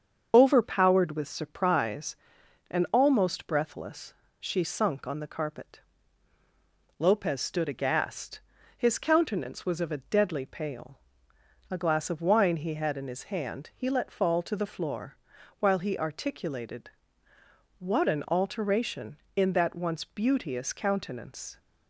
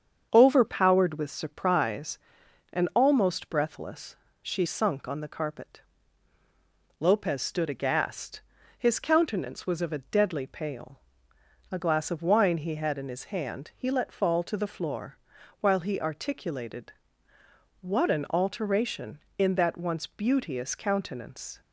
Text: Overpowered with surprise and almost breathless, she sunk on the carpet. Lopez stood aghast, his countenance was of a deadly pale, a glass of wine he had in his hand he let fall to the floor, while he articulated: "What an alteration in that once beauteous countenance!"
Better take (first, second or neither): second